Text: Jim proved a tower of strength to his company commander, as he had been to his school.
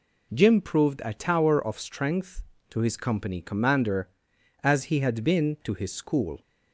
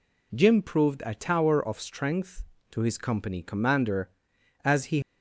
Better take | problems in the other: first | stops before "had been to his school"; at 5.0 s

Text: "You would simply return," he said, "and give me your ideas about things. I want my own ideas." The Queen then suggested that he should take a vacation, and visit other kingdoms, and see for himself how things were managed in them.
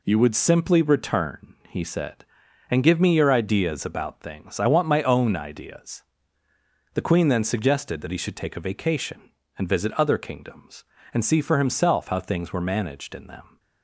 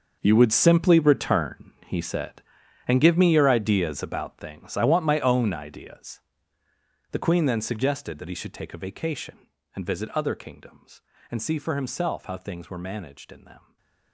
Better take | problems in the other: first | gets quieter; strong; throughout; 14.5 dB // stays silent after the last word; slight; from 13.5 s on; 0.6 s long

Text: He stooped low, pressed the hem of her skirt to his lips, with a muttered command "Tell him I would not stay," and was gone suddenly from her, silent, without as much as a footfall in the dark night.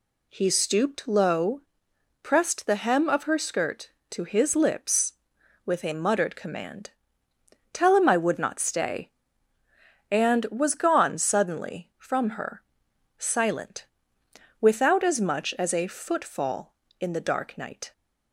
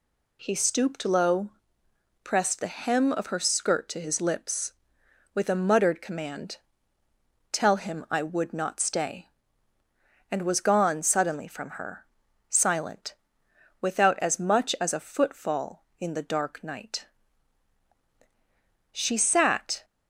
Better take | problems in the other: first | pauses between "command" and "Tell"; noticeable; at 6.5 s; 0.96 s long; noticeable in the first // goes on to say "She sat"; noticeable; from 18.9 s on; 0.92 s long

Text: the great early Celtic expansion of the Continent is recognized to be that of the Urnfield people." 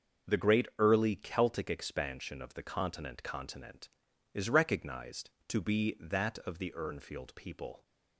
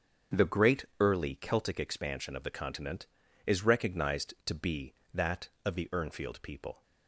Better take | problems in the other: second | starts louder than the rest; until 1.3 s; 6.5 dB; strong in the second // says "Continent" twice; at 3.2 s

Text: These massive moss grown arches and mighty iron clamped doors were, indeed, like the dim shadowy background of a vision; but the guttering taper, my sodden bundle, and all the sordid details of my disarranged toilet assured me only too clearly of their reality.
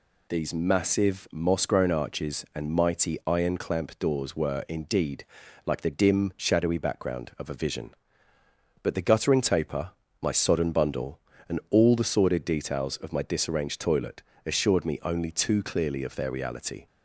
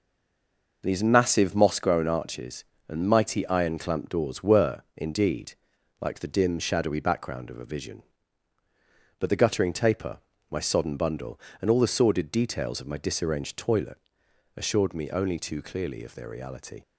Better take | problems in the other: first | stays silent before the first word; slight; until 0.8 s; 0.8 s long // pauses between "toilet" and "assured"; noticeable; at 13.9 s; 0.58 s long; slight in the first

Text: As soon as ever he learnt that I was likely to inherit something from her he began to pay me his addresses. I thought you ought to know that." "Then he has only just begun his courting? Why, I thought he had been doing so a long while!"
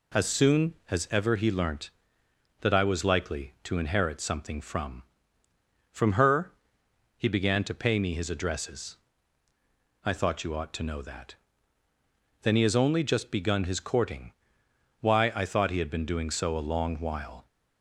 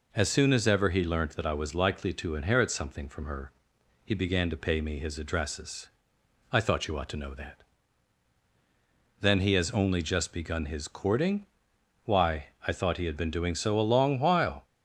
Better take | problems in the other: second | says "from" twice; at 5.9 s // pauses between "her" and "he"; noticeable; at 6.5 s; 0.64 s long; noticeable in the second

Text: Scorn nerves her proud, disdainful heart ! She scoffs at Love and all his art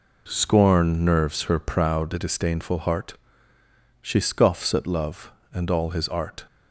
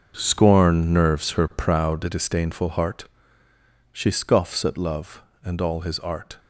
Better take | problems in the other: first | gets quieter; strong; throughout; 11.5 dB

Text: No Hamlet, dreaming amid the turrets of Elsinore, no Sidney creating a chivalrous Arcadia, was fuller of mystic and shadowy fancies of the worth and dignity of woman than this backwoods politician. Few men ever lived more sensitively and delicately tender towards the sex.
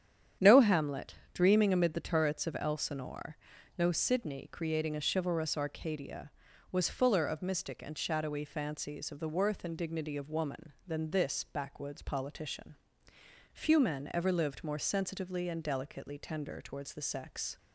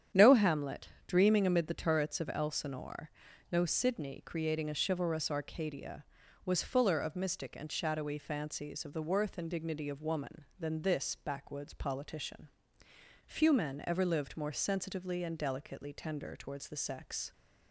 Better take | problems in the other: neither | starts louder than the rest; strong; the same in both

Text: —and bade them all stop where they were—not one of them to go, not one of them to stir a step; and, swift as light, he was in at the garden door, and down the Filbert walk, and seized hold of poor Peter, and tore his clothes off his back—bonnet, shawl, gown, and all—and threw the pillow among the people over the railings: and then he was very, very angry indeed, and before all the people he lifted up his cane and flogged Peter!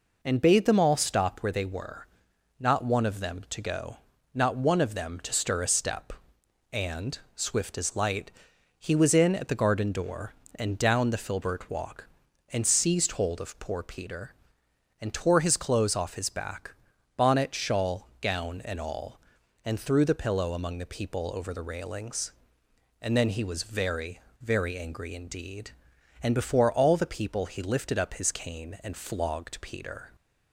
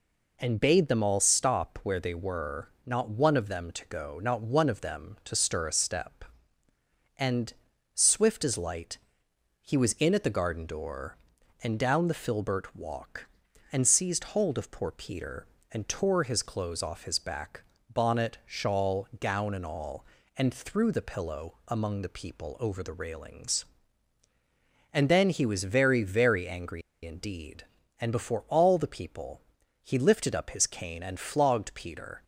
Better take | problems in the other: first | pauses between "angry" and "indeed"; slight; at 26.8 s; 0.23 s long // pauses between "people" and "he"; at 29.4 s; 0.40 s long

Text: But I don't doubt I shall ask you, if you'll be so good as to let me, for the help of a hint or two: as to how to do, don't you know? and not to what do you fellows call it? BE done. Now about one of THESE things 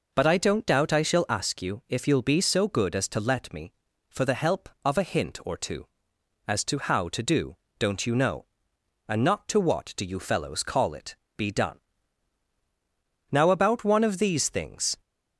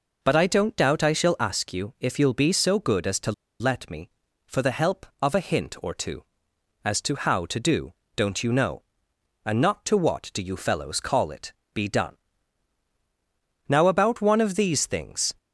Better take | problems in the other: first | pauses between "to" and "let"; slight; at 3.3 s; 0.28 s long

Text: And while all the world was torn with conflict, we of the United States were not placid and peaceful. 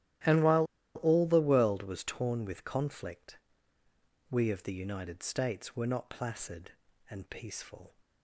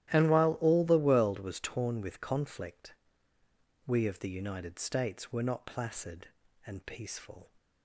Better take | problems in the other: second | starts louder than the rest; strong; until 1.5 s; 13 dB; strong in the second // pauses between "while" and "all"; slight; at 0.6 s; 0.29 s long

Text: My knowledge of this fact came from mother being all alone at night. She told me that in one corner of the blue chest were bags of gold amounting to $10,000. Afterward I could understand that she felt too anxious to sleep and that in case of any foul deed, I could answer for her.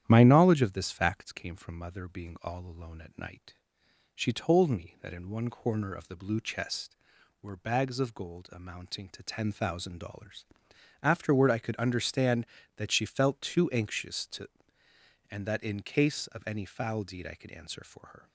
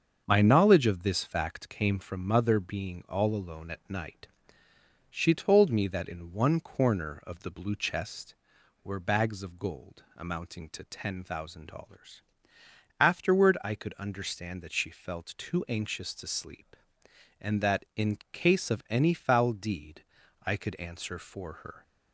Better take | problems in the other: second | starts louder than the rest; strong; until 1.0 s; 10.5 dB; also in the second // skips "sleep"; at 14.8 s

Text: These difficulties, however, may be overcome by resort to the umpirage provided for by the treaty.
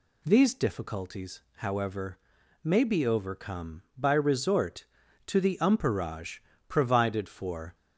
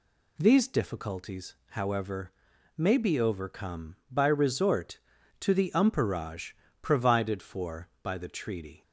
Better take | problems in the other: second | pauses between "umpirage" and "provided"; slight; at 6.3 s; 0.30 s long; slight in the second // stops before "by the treaty"; at 7.7 s

